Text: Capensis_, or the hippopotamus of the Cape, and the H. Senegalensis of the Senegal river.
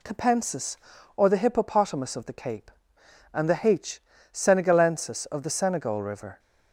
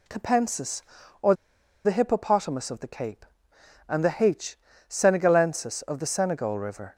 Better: first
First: none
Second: pauses between "or" and "the"; noticeable; at 1.3 s; 0.50 s long

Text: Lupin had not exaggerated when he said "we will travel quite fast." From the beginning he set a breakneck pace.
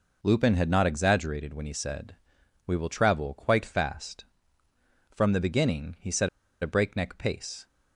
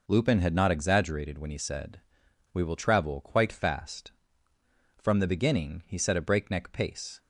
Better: second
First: pauses between "said" and "we"; noticeable; at 2.1 s; 0.50 s long // pauses between "set" and "a"; slight; at 6.2 s; 0.34 s long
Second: pauses between "said" and "we"; noticeable; at 1.9 s; 0.52 s long

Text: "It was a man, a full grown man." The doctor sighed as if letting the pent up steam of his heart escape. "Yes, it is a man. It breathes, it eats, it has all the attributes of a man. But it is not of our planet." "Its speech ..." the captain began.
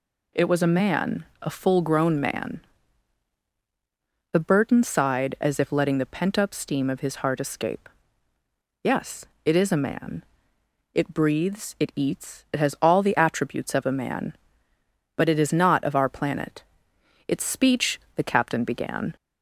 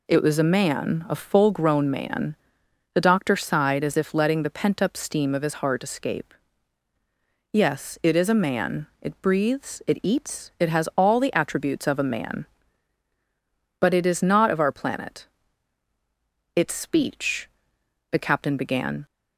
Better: second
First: says "burton" for "doctor"; at 4.3 s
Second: none

